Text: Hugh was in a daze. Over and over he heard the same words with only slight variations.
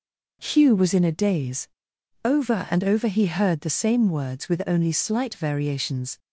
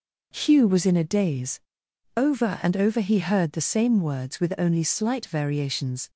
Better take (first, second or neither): neither